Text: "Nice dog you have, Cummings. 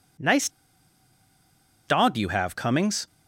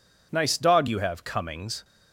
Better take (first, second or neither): second